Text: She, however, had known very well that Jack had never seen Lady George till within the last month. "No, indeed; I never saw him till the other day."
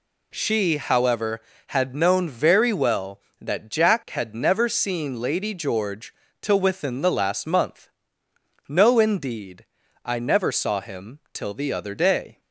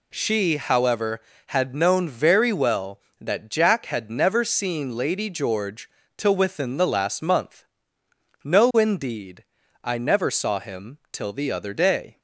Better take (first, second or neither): neither